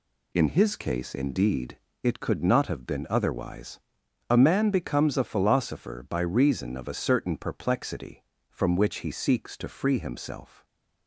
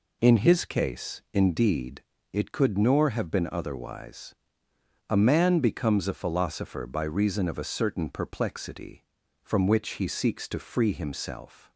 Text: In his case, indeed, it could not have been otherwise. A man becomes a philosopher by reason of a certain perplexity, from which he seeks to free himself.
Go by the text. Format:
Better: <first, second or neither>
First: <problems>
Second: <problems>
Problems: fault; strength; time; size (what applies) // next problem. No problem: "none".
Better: first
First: none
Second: says "nor" for "not"; at 2.7 s